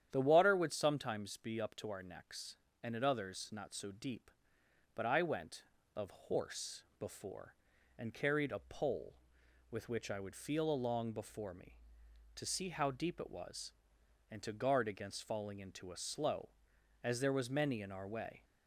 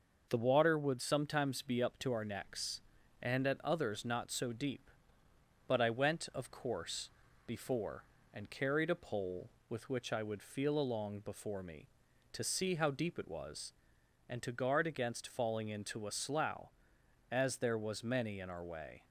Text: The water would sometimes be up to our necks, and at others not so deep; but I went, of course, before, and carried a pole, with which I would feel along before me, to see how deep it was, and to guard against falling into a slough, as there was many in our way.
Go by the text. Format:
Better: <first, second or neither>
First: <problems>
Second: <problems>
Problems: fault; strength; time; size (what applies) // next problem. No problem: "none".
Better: second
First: starts louder than the rest; strong; until 1.1 s; 10 dB // says "horse" for "course"; at 6.1 s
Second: none